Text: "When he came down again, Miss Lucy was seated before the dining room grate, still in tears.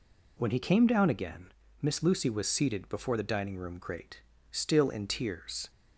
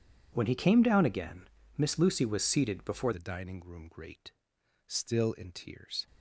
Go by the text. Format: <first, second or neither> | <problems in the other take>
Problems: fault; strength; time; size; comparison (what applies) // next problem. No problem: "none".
first | changes voice at "the"; from 3.1 s on; 2.9 s long